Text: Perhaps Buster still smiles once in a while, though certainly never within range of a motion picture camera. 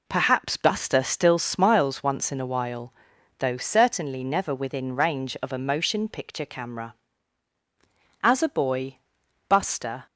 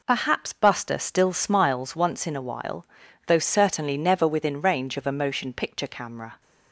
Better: second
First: goes on to say "As a boy Buster"; strong; from 8.2 s on; 1.8 s long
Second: none

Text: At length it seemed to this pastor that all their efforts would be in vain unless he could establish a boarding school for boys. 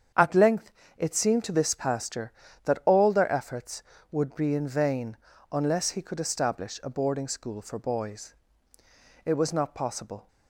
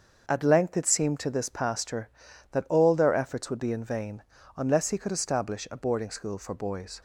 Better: second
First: starts louder than the rest; strong; until 1.4 s; 8 dB // pauses between "length" and "it"; slight; at 0.7 s; 0.28 s long // pauses between "vain" and "unless"; at 5.1 s; 0.38 s long // goes on to say "It was not possible"; noticeable; from 9.2 s on; 1.0 s long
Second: starts louder than the rest; until 1.2 s; 6.5 dB // pauses between "vain" and "unless"; slight; at 4.2 s; 0.34 s long

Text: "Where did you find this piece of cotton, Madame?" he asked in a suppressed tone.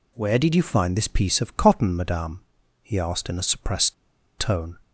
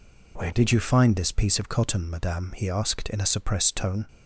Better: second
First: pauses between "suppressed" and "tone"; at 3.9 s; 0.44 s long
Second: none

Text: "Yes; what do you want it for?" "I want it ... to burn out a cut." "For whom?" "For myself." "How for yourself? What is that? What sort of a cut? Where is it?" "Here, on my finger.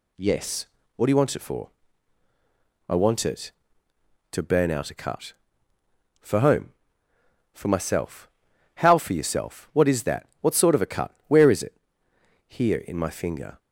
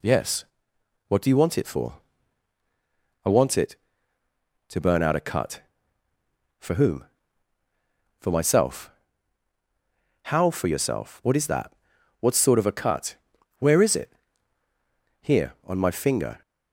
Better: second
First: says "in" for "on"; at 12.7 s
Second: none

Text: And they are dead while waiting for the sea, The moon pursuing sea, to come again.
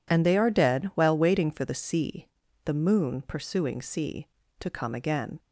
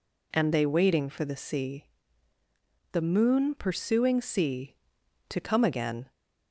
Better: first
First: none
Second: skips "are dead while"; at 0.6 s

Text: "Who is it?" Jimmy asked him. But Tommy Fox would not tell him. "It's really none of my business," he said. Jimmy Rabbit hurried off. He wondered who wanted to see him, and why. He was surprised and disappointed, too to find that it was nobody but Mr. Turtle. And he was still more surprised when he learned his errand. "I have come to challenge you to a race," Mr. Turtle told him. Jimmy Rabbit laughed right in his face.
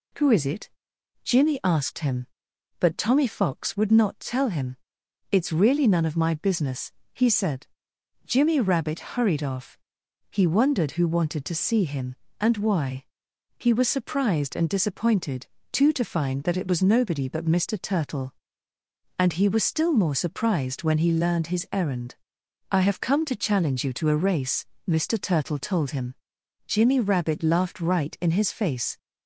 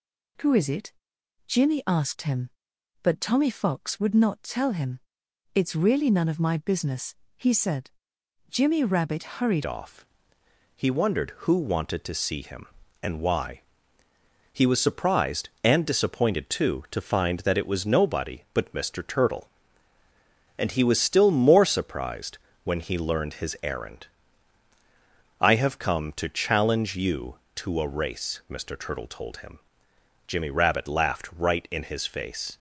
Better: first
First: none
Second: changes voice at "off"; from 9.6 s on; 22.9 s long // pauses between "surprised" and "when"; slight; at 22.3 s; 0.26 s long

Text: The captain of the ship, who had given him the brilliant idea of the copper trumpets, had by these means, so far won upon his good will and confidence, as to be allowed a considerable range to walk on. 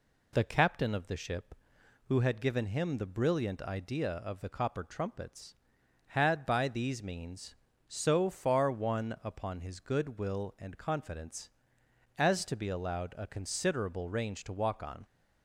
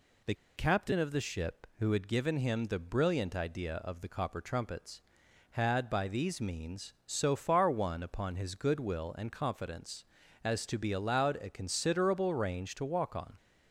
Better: first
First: none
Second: pauses between "The" and "captain"; slight; at 0.3 s; 0.21 s long

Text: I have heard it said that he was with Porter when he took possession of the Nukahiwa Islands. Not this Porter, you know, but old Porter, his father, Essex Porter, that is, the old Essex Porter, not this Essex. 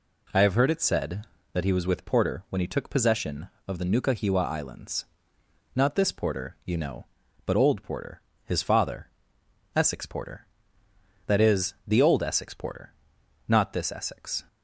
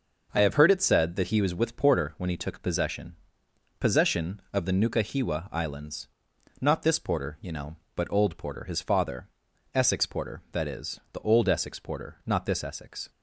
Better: first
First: none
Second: says "possession" twice; at 3.8 s

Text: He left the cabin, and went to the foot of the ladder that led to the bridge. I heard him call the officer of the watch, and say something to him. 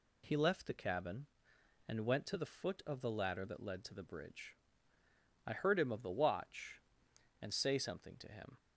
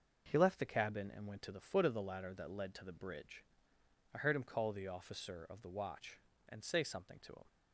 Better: second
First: skips "call the officer"; at 5.9 s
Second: none

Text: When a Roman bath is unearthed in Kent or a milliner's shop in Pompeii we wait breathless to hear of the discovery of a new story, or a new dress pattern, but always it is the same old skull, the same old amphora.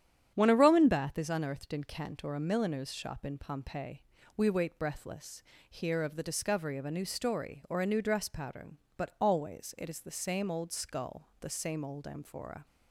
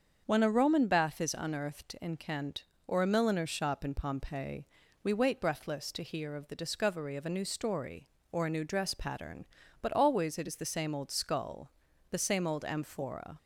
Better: second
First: starts louder than the rest; strong; until 1.3 s; 9 dB // pauses between "Pompeii" and "we"; slight; at 4.0 s; 0.34 s long // skips "to"; at 5.5 s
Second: starts louder than the rest; until 1.2 s; 7 dB // pauses between "Pompeii" and "we"; at 4.6 s; 0.38 s long

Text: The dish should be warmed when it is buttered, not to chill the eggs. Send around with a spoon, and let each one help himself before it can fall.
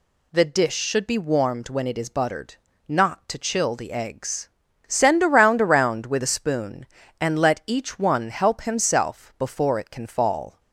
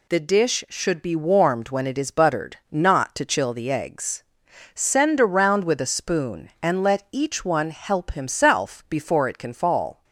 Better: second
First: says "around" twice; at 5.6 s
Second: none

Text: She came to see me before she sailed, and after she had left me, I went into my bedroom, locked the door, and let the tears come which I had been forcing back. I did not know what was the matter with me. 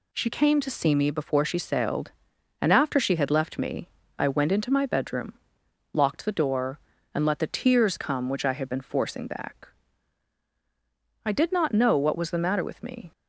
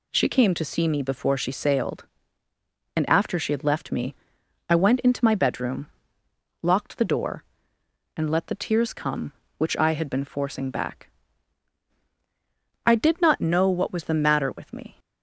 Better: neither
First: none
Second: none

